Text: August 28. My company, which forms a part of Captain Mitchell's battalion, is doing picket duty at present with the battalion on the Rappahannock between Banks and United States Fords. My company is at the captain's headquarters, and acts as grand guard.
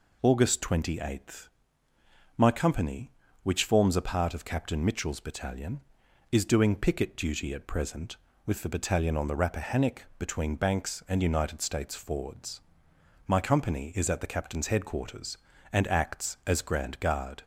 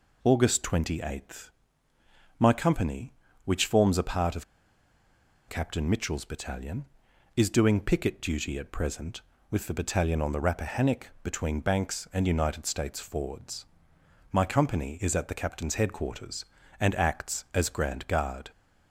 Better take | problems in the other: first | pauses between "of" and "Captain"; at 4.4 s; 1.0 s long

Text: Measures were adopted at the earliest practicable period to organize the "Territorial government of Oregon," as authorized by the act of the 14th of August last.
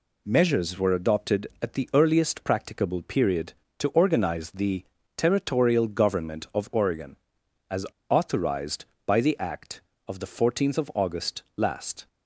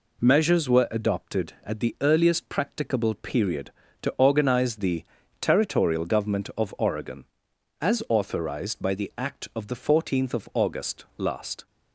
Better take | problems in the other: second | pauses between "the" and "Territorial"; slight; at 4.8 s; 0.32 s long; slight in the second // pauses between "as" and "authorized"; slight; at 7.8 s; 0.24 s long

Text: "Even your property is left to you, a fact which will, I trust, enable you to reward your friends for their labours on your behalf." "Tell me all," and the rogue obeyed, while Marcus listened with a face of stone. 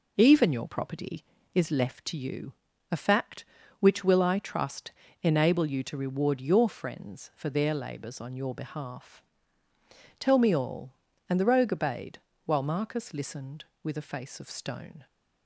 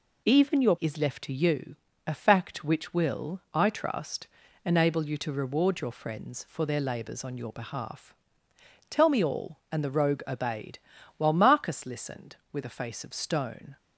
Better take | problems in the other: first | skips "property"; at 0.7 s

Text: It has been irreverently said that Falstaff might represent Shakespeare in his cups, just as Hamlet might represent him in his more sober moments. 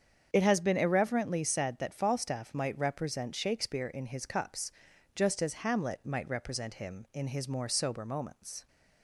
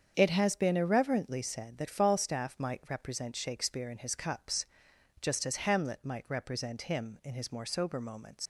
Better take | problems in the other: first | starts louder than the rest; strong; until 1.1 s; 7.5 dB; strong in the first // leaves "moments" unfinished; at 8.4 s; 90 ms

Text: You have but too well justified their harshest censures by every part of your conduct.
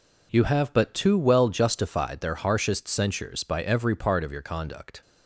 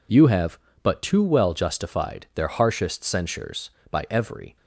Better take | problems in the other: first | stops before "part of your conduct"; at 4.5 s

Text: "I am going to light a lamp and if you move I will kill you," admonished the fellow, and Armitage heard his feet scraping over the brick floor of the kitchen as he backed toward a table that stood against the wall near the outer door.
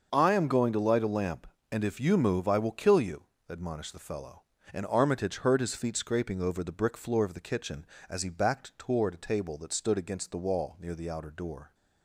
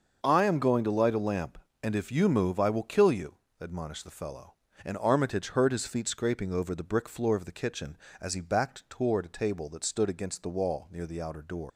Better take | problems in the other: first | starts louder than the rest; until 1.2 s; 6.5 dB; also in the first // leaves "door" unfinished; at 11.6 s; 155 ms

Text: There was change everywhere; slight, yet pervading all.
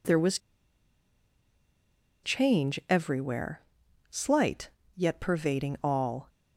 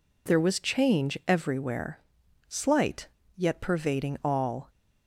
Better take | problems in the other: second | pauses between "was" and "change"; strong; at 0.3 s; 1.8 s long

